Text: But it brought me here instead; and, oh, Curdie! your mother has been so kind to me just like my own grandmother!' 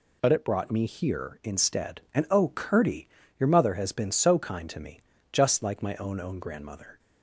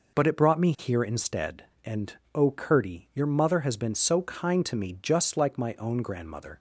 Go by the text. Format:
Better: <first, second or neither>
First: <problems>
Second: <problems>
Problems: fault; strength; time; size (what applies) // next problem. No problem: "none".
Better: second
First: pauses between "me" and "just"; slight; at 4.9 s; 0.32 s long // says "own" twice; at 6.1 s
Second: none